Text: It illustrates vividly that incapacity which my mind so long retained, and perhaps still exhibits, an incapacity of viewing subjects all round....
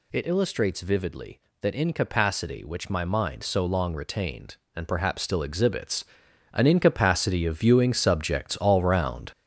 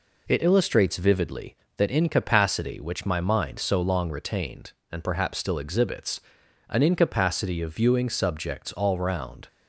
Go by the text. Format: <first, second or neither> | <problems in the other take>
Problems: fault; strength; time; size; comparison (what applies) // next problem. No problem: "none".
second | gets louder; throughout; 6.5 dB